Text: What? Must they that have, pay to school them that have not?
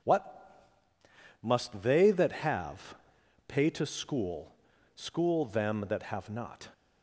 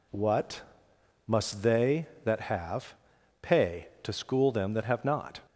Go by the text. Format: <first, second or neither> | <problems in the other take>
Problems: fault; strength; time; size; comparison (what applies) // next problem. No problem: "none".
second | says "school" twice; at 4.9 s